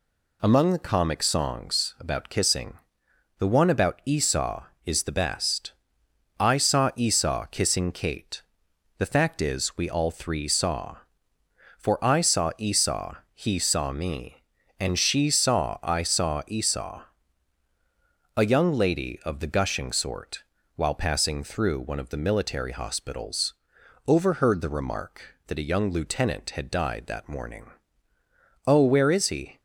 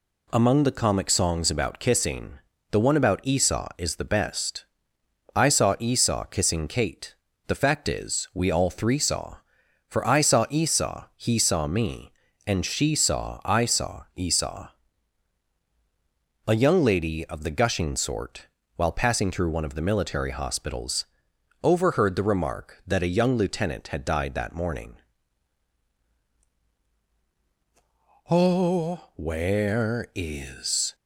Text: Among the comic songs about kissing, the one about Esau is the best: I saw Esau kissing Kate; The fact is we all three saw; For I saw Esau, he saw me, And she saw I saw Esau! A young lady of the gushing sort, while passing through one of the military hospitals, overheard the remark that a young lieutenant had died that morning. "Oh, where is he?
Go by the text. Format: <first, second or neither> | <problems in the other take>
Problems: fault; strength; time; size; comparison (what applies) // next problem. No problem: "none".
first | stops before "he"; at 30.9 s